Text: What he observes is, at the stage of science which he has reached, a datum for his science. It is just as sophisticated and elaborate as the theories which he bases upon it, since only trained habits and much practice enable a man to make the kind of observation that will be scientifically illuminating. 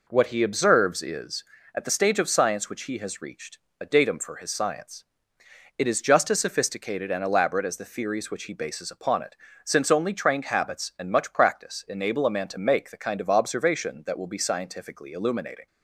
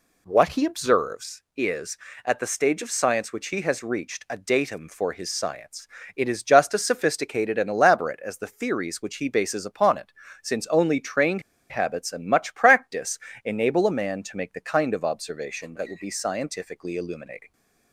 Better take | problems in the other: first | pauses between "trained" and "habits"; slight; at 11.4 s; 0.28 s long // pauses between "practice" and "enable"; slight; at 13.1 s; 0.28 s long

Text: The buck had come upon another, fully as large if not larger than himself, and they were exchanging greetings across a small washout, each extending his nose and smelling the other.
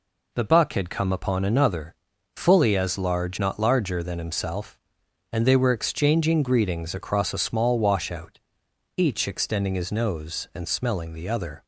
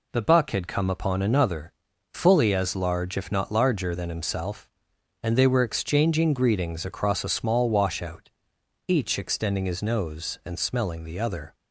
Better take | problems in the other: second | skips "if"; at 3.3 s

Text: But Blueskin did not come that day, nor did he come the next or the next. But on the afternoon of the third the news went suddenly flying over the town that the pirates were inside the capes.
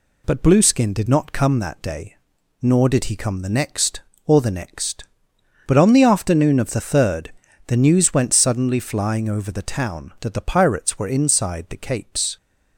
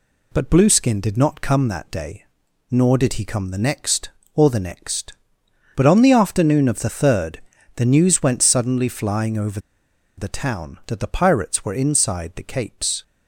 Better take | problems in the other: first | pauses between "third" and "the"; slight; at 7.4 s; 0.36 s long; slight in the first // pauses between "over" and "the"; noticeable; at 9.5 s; 0.59 s long

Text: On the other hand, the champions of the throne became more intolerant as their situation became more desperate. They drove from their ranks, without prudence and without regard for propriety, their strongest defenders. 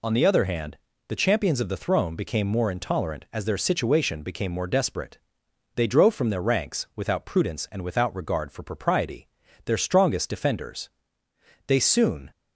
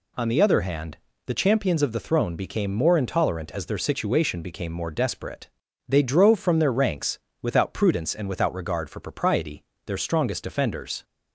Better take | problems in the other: second | goes on to say "They soon"; noticeable; from 11.6 s on; 0.64 s long

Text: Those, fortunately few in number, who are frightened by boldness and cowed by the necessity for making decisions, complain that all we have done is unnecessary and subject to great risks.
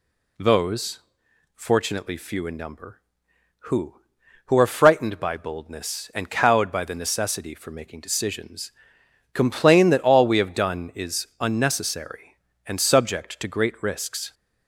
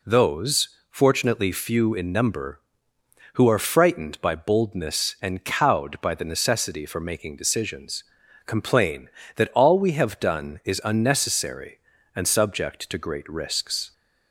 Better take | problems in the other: second | says "who" twice; at 4.4 s

